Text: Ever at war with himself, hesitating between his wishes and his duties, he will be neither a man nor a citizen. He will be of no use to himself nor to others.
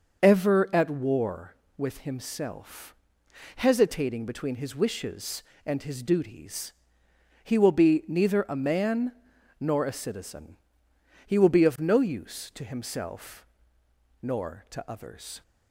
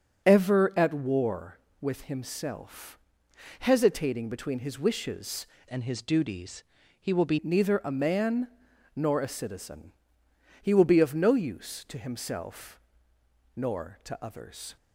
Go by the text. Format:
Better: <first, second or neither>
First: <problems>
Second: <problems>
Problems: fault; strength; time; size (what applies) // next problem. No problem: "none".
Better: first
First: starts louder than the rest; until 1.2 s; 6 dB // pauses between "man" and "nor"; noticeable; at 9.1 s; 0.48 s long // pauses between "himself" and "nor"; noticeable; at 13.4 s; 0.74 s long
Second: starts louder than the rest; until 1.3 s; 6.5 dB // changes voice from "and" to "be"; from 5.6 to 7.3 s; 1.7 s long // pauses between "man" and "nor"; noticeable; at 8.4 s; 0.48 s long // pauses between "himself" and "nor"; noticeable; at 12.7 s; 0.74 s long